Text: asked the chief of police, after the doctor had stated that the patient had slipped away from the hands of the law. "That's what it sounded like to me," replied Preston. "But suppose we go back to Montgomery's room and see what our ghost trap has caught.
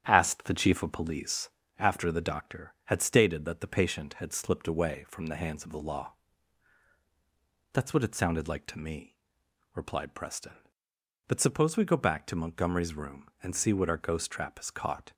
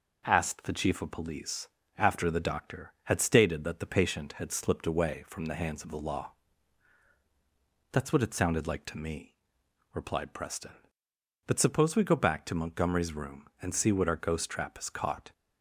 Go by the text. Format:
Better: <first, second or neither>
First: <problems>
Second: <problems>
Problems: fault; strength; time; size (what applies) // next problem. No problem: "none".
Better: second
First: starts louder than the rest; strong; until 1.7 s; 9.5 dB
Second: none